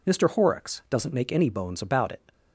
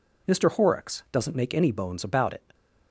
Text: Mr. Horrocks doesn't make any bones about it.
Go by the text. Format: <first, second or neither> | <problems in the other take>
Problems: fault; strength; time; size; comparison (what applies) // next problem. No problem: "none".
neither | none